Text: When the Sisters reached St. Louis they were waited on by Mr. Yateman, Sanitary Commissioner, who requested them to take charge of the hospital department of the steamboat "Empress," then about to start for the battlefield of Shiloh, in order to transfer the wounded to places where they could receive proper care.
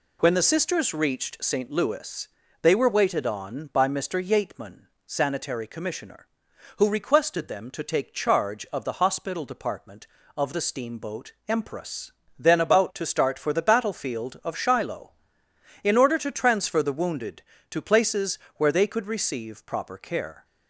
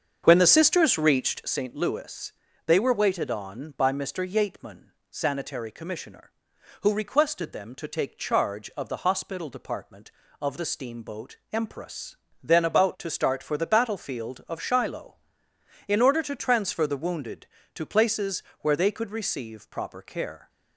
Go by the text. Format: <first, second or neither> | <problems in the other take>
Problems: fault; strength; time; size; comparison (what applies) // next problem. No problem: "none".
first | starts louder than the rest; until 1.5 s; 7 dB // pauses between "Louis" and "they"; slight; at 2.3 s; 0.32 s long; slight in the first // pauses between "steamboat" and "Empress"; slight; at 11.3 s; 0.16 s long; slight in the first // pauses between "places" and "where"; slight; at 18.4 s; 0.18 s long; slight in the first